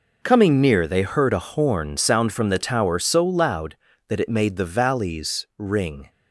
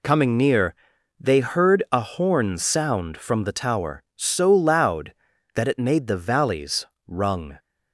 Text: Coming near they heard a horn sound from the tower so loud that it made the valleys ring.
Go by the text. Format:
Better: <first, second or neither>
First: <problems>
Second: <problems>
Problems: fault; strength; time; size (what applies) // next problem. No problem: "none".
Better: first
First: none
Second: pauses between "near" and "they"; noticeable; at 0.7 s; 0.46 s long // says "rung" for "ring"; at 7.0 s